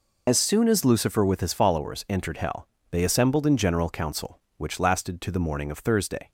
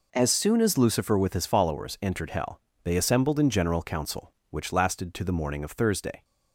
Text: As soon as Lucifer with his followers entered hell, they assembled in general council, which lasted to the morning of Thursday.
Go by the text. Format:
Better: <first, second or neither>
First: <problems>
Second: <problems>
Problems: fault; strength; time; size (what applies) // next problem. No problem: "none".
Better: second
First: loses the start of "As"; at 0.2 s; 80 ms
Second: none